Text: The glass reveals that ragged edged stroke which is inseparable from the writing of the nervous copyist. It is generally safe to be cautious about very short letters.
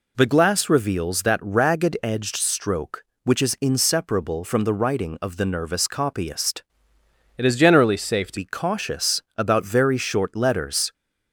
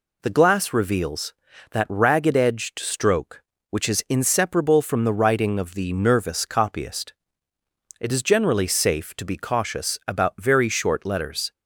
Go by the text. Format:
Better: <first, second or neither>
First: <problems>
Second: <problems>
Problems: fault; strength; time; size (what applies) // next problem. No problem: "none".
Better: second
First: changes voice from "It" to "to"; from 7.3 to 8.3 s; 1.0 s long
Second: none